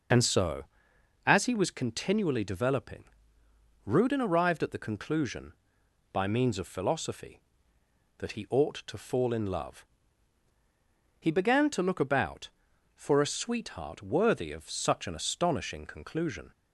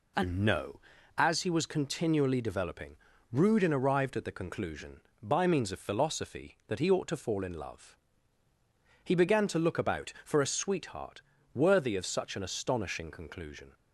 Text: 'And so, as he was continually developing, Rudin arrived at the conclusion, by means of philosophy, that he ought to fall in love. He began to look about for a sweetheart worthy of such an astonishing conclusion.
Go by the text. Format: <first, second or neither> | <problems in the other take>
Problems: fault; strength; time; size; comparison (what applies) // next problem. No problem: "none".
first | says "no" for "so"; at 0.3 s // pauses between "sweetheart" and "worthy"; slight; at 11.2 s; 0.32 s long